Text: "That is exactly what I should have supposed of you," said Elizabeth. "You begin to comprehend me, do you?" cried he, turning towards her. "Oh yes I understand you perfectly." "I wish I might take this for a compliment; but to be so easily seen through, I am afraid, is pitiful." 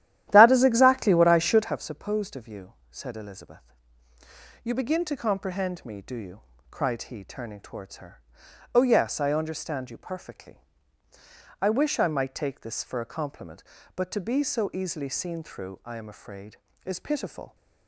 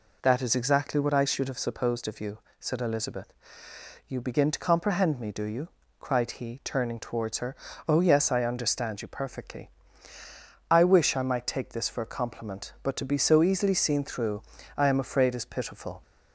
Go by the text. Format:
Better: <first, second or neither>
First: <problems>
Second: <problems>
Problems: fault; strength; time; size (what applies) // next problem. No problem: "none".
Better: second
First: starts louder than the rest; strong; until 1.8 s; 12.5 dB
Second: none